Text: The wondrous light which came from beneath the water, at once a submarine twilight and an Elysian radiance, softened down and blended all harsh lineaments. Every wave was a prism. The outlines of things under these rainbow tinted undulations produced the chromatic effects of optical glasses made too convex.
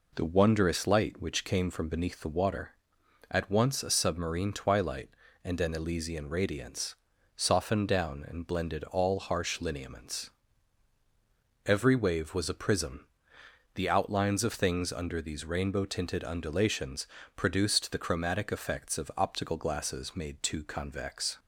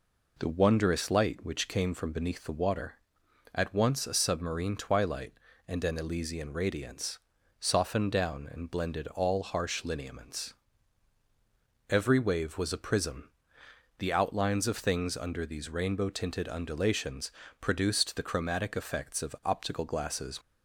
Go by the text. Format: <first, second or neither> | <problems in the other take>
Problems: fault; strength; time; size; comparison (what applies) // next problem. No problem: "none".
first | pauses between "undulations" and "produced"; slight; at 17.3 s; 0.28 s long; slight in the first // stops before "made too convex"; at 20.4 s